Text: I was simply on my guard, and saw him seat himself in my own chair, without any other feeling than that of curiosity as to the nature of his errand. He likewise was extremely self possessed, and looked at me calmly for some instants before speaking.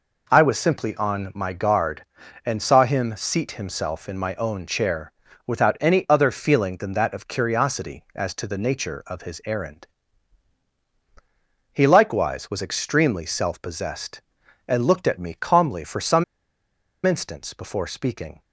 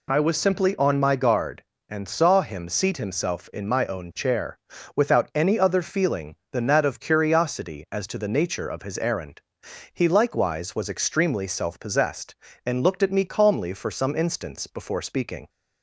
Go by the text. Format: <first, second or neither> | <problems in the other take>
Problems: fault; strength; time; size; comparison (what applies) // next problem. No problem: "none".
second | pauses between "some" and "instants"; noticeable; at 16.2 s; 0.82 s long